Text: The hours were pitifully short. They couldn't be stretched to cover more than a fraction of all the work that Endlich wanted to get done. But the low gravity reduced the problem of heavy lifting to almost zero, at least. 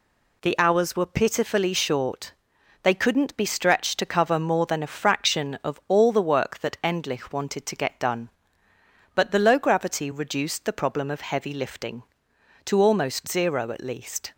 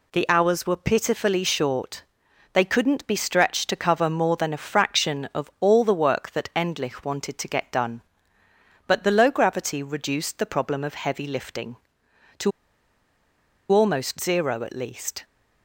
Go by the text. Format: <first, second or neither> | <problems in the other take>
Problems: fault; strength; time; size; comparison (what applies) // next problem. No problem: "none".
first | pauses between "to" and "almost"; at 12.5 s; 1.2 s long